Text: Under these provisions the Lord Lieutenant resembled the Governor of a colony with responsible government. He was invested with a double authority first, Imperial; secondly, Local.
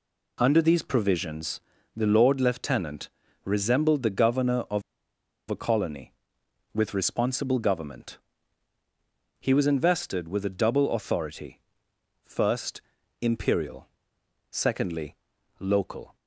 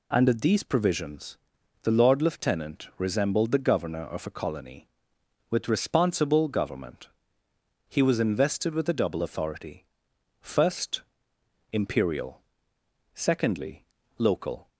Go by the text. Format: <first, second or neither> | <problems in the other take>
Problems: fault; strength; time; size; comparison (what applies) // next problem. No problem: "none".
second | pauses between "provisions" and "the"; at 1.5 s; 0.38 s long; noticeable in the second // pauses between "Lieutenant" and "resembled"; slight; at 3.0 s; 0.34 s long // pauses between "of" and "a"; noticeable; at 4.8 s; 0.69 s long // pauses between "authority" and "first"; noticeable; at 11.6 s; 0.62 s long; noticeable in the second